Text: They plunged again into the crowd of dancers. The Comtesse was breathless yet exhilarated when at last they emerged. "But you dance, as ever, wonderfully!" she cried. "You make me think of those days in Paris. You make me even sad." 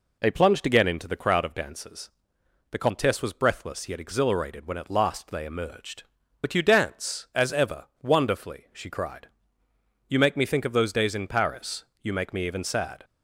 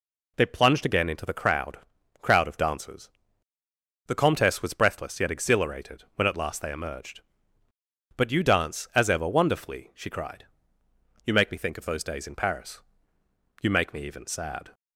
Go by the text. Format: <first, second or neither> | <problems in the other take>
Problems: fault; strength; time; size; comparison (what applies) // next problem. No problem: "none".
first | says "crowd" twice; at 2.2 s